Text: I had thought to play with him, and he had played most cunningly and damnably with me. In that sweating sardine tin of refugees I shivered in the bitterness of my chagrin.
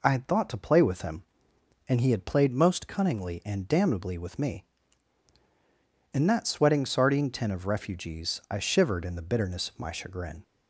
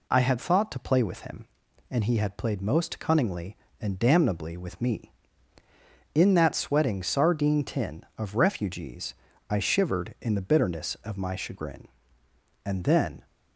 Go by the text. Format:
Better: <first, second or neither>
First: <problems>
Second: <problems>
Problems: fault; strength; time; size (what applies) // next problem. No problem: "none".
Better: first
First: none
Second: pauses between "refugees" and "I"; slight; at 9.1 s; 0.36 s long // goes on to say "And then"; noticeable; from 12.6 s on; 0.62 s long